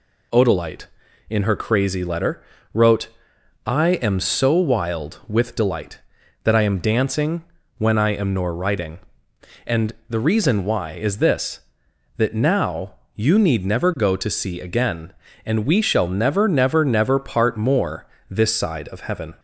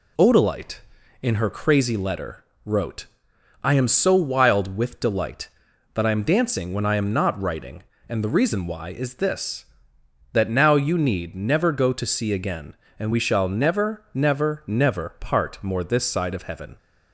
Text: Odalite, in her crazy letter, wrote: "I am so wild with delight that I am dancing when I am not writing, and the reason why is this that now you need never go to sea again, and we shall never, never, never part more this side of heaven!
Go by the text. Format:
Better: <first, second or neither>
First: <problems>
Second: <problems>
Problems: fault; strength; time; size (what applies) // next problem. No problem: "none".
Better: second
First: pauses between "dancing" and "when"; slight; at 7.4 s; 0.34 s long // says "nor" for "not"; at 8.3 s // pauses between "and" and "the"; slight; at 9.9 s; 0.18 s long // pauses between "now" and "you"; slight; at 12.9 s; 0.20 s long // pauses between "more" and "this"; slight; at 18.0 s; 0.22 s long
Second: none